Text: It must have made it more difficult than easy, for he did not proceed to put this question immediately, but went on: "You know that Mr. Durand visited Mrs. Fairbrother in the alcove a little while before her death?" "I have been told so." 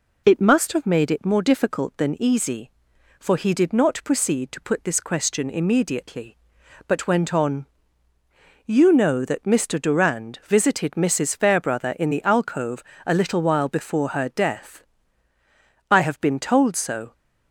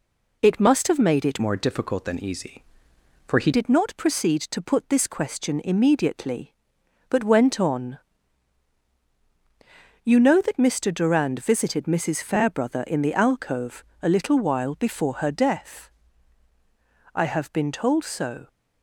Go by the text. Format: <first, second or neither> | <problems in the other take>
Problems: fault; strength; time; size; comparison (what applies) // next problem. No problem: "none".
first | changes voice from "more" to "he"; from 1.4 to 3.5 s; 2.1 s long // pauses between "alcove" and "a"; slight; at 13.8 s; 0.18 s long; slight in the first